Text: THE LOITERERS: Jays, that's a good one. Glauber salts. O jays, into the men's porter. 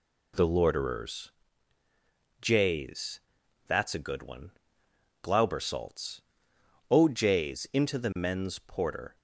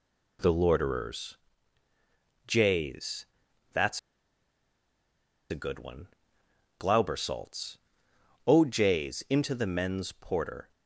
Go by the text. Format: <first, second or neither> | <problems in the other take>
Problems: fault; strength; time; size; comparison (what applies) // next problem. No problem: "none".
first | pauses between "that's" and "a"; strong; at 3.9 s; 1.5 s long